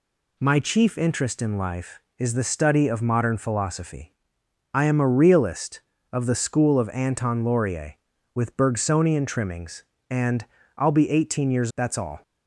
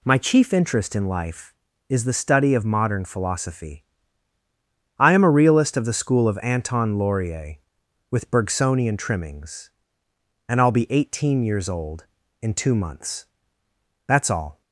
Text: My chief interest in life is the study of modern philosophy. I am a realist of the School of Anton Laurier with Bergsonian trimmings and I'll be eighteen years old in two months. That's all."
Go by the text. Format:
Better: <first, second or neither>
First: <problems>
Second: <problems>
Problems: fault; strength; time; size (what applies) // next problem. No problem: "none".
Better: second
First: pauses between "and" and "I'll"; slight; at 10.4 s; 0.32 s long // skips "old in two months"; at 11.7 s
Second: none